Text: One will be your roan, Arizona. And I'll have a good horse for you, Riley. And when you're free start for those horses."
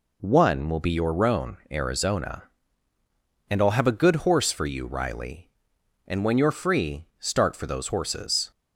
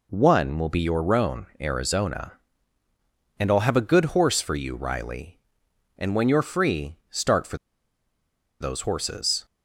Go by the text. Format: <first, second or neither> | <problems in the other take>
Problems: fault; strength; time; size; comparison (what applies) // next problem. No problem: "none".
first | pauses between "free" and "start"; slight; at 6.9 s; 0.16 s long; slight in the first // pauses between "for" and "those"; at 7.5 s; 1.0 s long